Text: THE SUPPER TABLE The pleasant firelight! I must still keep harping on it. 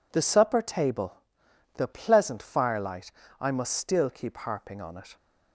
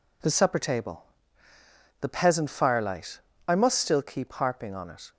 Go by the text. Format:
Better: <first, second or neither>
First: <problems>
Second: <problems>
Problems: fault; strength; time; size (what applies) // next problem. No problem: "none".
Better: first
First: pauses between "TABLE" and "The"; noticeable; at 1.1 s; 0.60 s long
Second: pauses between "TABLE" and "The"; noticeable; at 1.0 s; 0.98 s long // says "peasant" for "pleasant"; at 2.0 s